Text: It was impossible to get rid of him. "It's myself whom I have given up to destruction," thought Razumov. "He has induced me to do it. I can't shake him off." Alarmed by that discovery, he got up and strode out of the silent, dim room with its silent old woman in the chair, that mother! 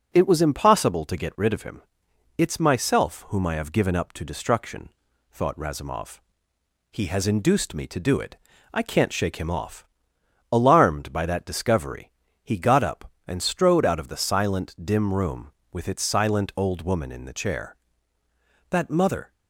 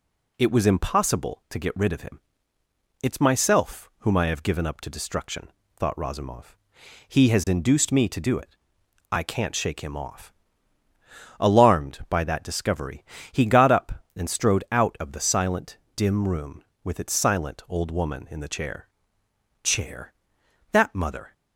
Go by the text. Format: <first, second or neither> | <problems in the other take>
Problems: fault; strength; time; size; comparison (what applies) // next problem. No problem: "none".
first | says "chair" twice; at 19.6 s